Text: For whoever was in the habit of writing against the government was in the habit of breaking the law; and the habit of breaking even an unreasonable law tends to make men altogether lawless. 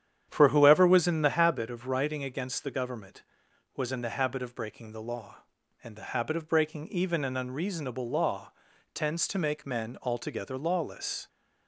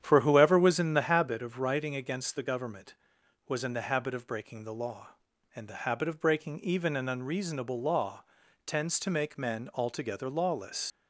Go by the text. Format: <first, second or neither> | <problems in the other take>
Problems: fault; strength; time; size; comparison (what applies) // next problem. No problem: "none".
first | starts louder than the rest; strong; until 1.0 s; 9.5 dB; strong in the first // pauses between "law" and "tends"; at 8.2 s; 0.42 s long; also in the first // leaves "lawless" unfinished; at 10.9 s; 95 ms